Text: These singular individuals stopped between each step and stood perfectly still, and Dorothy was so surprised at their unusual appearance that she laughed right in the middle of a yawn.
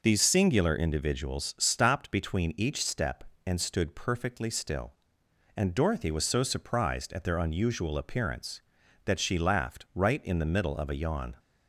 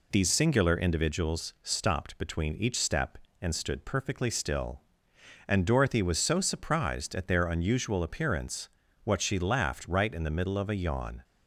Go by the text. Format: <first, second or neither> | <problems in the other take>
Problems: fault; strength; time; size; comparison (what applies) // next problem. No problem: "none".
first | says "what" for "that"; at 9.0 s